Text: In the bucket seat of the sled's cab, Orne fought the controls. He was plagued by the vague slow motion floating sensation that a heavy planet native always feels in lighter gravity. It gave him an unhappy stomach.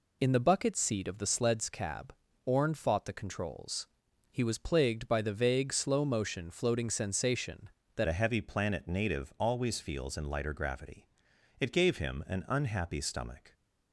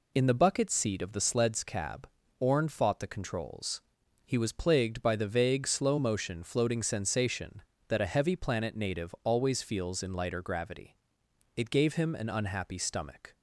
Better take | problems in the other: second | changes voice at "a"; from 8.0 s on; 5.5 s long

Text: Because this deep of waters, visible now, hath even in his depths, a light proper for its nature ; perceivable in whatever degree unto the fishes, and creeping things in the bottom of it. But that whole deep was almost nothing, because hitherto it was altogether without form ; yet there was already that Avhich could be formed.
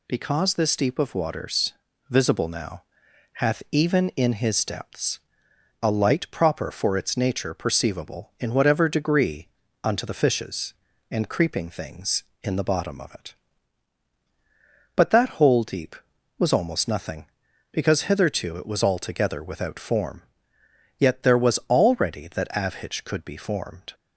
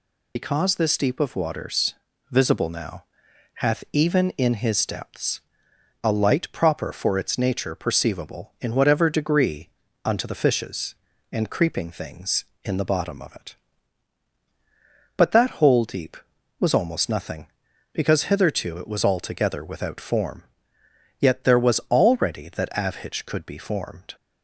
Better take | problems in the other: first | loses the start of "Because"; at 0.3 s; 60 ms // pauses between "degree" and "unto"; slight; at 9.6 s; 0.34 s long; slight in the first

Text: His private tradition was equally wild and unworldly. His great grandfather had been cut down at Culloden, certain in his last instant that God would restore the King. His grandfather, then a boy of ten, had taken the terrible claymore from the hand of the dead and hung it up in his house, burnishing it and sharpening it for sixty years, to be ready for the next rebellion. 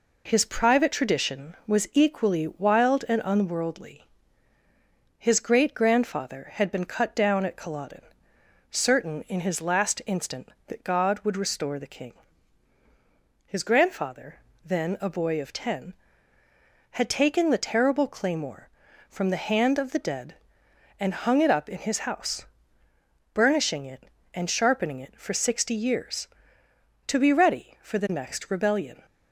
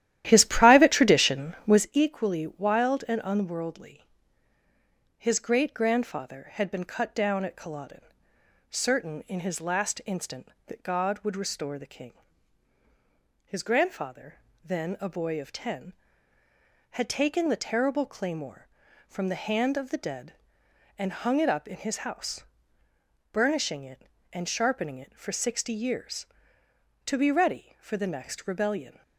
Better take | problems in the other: first | starts louder than the rest; strong; until 1.9 s; 13 dB

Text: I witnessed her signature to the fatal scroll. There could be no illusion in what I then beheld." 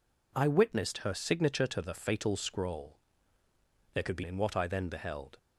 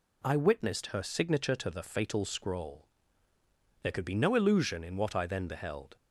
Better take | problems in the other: second | skips "no illusion"; at 4.2 s

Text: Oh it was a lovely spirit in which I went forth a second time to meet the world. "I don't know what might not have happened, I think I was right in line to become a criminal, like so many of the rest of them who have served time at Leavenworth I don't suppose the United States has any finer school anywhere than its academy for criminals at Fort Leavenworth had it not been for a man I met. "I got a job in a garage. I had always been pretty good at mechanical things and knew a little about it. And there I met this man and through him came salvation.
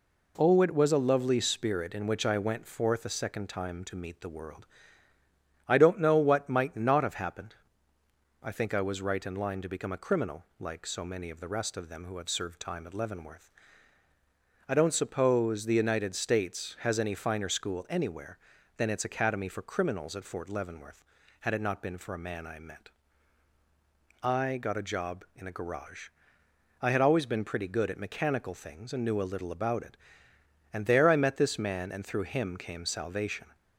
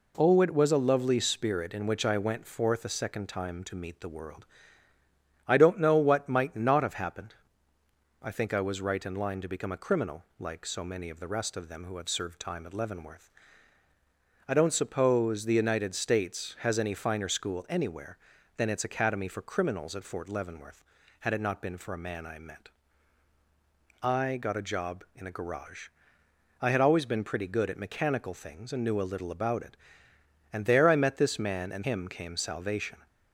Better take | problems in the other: first | pauses between "Leavenworth" and "I"; at 13.2 s; 1.1 s long; also in the first // skips "through"; at 31.8 s

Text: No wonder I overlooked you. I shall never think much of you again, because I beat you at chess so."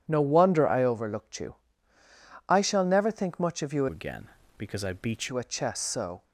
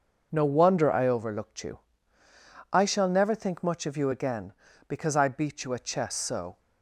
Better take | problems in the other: second | changes voice from "again" to "beat"; from 3.8 to 5.2 s; 1.4 s long

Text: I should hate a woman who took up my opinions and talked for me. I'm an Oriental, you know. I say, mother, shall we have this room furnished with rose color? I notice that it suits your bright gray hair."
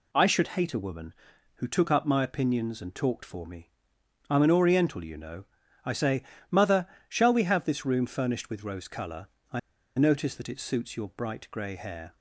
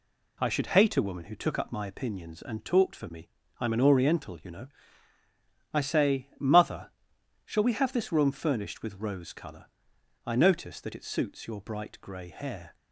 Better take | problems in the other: second | pauses between "I" and "notice"; at 9.5 s; 0.38 s long

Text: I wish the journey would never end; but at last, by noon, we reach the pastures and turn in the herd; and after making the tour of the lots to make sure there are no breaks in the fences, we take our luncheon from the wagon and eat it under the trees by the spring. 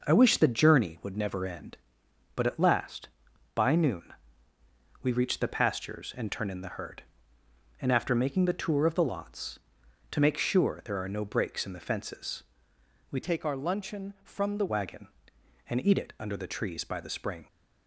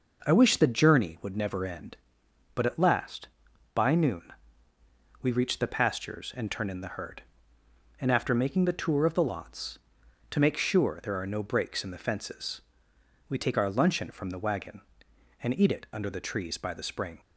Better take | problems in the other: second | changes voice from "take" to "the"; from 13.2 to 14.6 s; 1.4 s long

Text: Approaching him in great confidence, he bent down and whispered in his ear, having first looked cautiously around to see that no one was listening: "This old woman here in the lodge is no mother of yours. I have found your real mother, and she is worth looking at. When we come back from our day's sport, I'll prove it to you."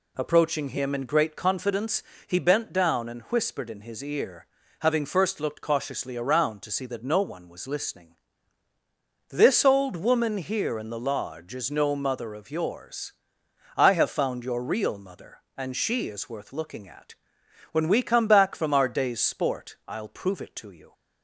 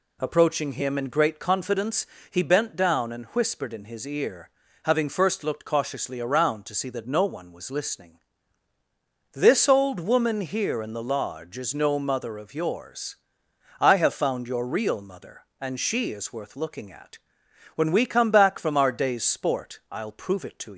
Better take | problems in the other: first | stops before "you"; at 20.7 s

